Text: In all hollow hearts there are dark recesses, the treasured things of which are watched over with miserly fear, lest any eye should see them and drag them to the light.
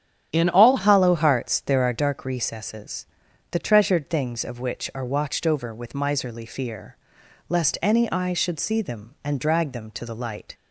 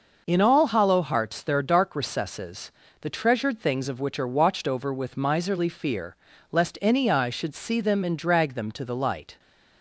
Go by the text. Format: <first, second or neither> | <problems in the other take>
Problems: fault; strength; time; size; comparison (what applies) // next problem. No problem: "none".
second | starts louder than the rest; strong; until 1.3 s; 9.5 dB // changes voice at "hollow"; from 0.7 s on; 9.8 s long